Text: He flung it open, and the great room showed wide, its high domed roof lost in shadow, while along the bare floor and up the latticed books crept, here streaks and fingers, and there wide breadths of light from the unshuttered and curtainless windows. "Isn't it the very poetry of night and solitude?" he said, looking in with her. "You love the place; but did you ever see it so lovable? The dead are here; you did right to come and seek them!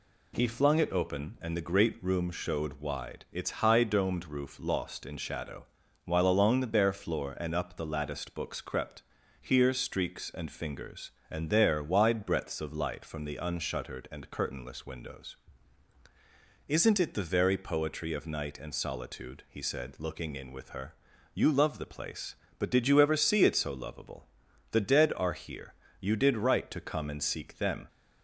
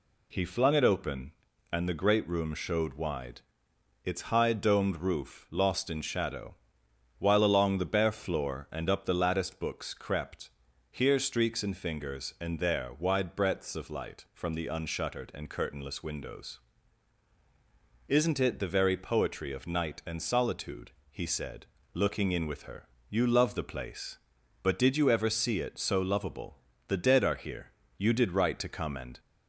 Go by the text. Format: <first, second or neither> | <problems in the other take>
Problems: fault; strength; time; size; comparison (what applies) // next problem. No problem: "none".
first | stops before "seek them"; at 29.1 s